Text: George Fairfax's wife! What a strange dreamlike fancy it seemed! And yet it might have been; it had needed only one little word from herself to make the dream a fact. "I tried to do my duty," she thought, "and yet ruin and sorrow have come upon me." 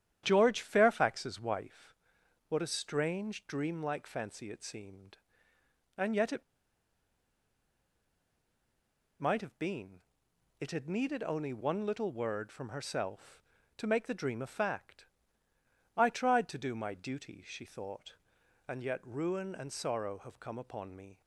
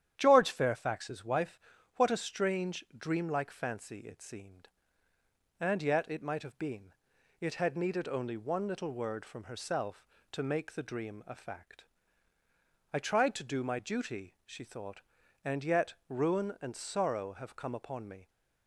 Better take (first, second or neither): second